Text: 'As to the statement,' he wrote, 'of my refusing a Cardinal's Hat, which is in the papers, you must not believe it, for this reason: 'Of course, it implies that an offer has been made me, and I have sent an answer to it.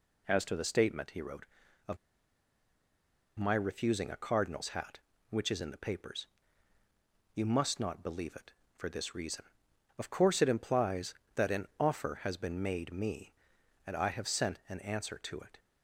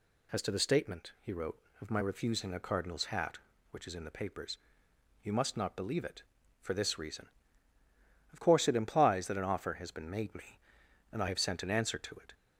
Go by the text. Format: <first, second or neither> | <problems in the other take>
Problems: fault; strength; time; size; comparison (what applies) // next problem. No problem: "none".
second | pauses between "of" and "my"; strong; at 1.9 s; 1.4 s long